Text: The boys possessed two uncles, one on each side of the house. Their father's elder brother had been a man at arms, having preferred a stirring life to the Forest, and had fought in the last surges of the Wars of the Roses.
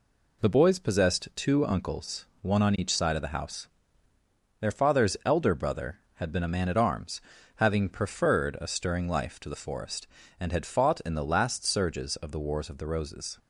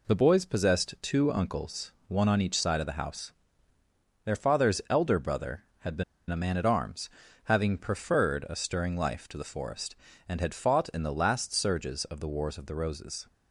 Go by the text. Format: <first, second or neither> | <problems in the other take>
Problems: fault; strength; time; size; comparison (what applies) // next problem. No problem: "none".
first | pauses between "been" and "a"; slight; at 6.0 s; 0.25 s long